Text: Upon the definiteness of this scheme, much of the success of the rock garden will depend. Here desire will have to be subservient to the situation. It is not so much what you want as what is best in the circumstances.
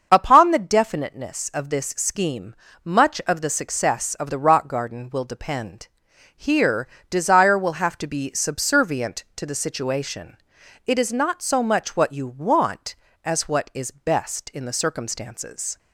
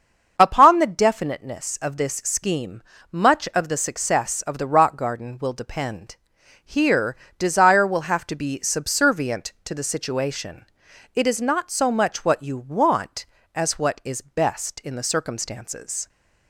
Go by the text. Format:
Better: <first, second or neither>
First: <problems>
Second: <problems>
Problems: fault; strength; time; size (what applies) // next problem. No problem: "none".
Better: neither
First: starts louder than the rest; until 1.1 s; 6.5 dB // pauses between "Here" and "desire"; slight; at 6.8 s; 0.22 s long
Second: starts louder than the rest; until 1.3 s; 6.5 dB // pauses between "Here" and "desire"; slight; at 7.1 s; 0.22 s long